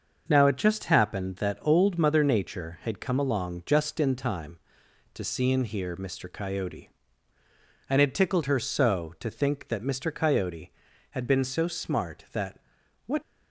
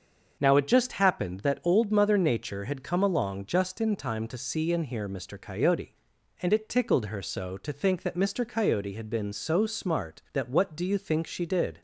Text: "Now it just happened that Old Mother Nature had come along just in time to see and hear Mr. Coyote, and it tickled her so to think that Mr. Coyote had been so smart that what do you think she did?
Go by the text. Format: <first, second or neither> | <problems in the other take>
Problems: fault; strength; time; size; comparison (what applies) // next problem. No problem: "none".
second | starts louder than the rest; until 1.2 s; 6 dB; also in the second // pauses between "that" and "what"; noticeable; at 12.5 s; 0.46 s long // stops before "do you think she did"; at 13.2 s